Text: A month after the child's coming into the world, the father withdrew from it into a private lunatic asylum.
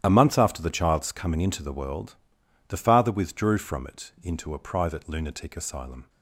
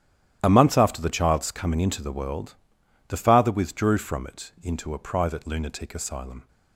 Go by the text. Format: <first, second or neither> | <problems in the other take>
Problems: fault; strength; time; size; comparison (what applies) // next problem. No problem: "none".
neither | starts louder than the rest; strong; the same in both